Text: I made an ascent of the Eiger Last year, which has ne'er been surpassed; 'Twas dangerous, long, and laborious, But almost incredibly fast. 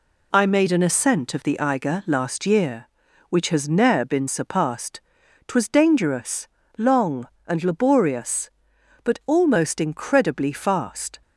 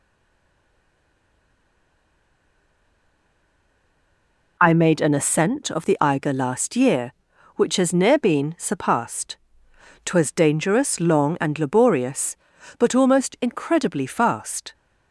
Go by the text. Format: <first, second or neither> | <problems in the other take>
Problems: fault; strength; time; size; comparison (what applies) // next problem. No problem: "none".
first | stays silent before the first word; strong; until 4.5 s; 4.5 s long